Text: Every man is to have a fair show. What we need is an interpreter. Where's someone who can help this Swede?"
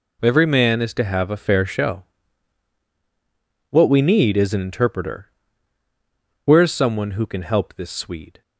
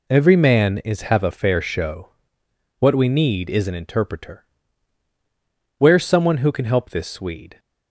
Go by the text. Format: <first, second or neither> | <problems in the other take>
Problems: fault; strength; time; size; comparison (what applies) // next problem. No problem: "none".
first | skips "to"; at 1.0 s